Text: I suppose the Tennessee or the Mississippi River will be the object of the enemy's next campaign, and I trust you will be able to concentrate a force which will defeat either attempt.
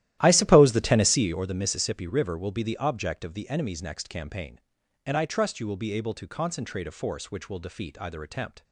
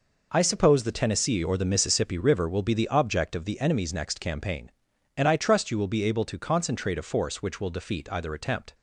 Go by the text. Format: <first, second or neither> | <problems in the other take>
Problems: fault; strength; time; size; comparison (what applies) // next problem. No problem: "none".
second | starts louder than the rest; strong; until 1.4 s; 13.5 dB